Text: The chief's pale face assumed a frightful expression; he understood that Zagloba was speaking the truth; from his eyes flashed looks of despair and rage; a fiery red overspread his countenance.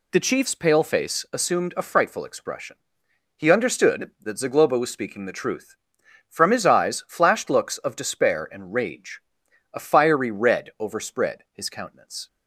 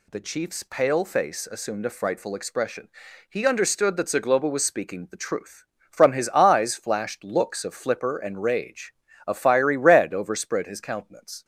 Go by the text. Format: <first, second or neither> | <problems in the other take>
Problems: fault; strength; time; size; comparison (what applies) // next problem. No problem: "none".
first | says "flipper" for "despair"; at 7.7 s